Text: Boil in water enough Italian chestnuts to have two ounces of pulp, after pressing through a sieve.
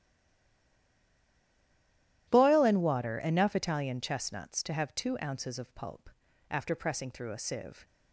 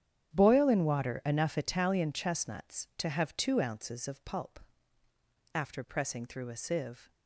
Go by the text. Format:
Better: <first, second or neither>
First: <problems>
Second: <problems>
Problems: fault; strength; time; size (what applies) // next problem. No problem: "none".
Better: second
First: stays silent before the first word; until 2.2 s; 2.2 s long // starts louder than the rest; strong; until 3.3 s; 12.5 dB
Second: starts louder than the rest; strong; until 1.3 s; 9.5 dB